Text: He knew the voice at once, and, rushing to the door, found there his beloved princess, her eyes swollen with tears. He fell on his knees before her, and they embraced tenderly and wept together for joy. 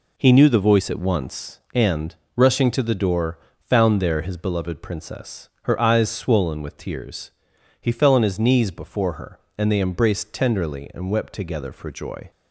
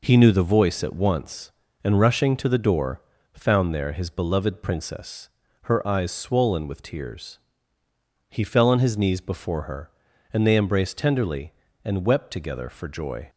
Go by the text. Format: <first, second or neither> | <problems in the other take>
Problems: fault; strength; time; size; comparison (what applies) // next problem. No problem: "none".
neither | none